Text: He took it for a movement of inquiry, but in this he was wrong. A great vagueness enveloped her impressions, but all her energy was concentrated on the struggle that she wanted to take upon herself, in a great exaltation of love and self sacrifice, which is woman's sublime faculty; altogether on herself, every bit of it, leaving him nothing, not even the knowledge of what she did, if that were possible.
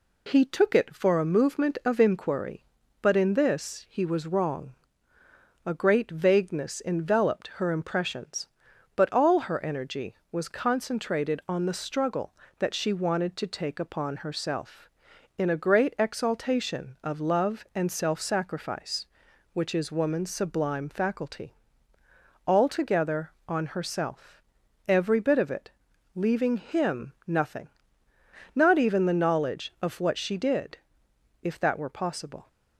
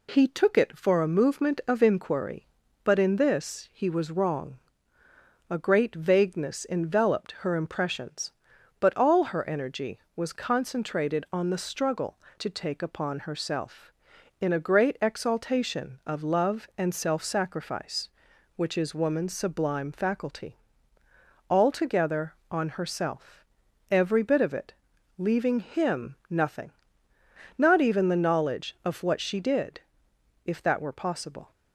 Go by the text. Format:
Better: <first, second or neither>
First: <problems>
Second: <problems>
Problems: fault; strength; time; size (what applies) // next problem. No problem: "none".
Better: first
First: none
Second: skips "that she wanted"; at 12.2 s